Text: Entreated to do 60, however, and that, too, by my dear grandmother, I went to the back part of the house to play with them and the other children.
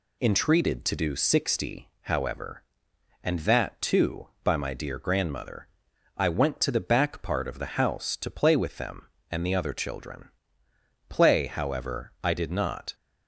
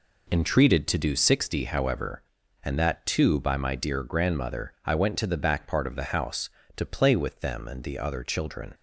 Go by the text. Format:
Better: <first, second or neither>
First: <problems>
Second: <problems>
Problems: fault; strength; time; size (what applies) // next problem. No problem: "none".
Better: second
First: goes on to say "Play however I did not"; strong; from 11.0 s on; 1.8 s long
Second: none